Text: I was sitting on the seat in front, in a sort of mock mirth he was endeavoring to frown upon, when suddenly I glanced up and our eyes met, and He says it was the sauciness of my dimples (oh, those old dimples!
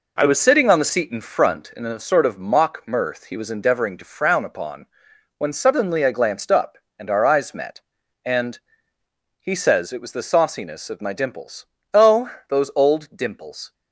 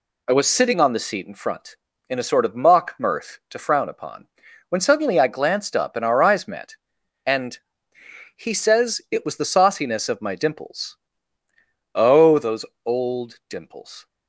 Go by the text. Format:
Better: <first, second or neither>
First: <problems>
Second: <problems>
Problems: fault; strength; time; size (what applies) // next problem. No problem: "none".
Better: first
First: pauses between "and" and "He"; noticeable; at 8.5 s; 0.82 s long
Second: skips "he was endeavoring"; at 3.4 s // pauses between "and" and "He"; noticeable; at 7.5 s; 0.76 s long // pauses between "those" and "old"; slight; at 12.6 s; 0.22 s long